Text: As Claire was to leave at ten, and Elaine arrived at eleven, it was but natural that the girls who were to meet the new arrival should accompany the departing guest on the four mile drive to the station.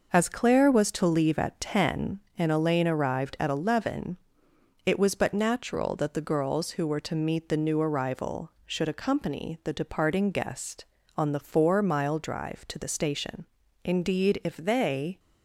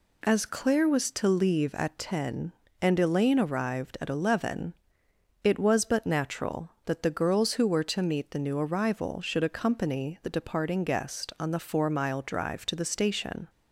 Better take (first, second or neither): second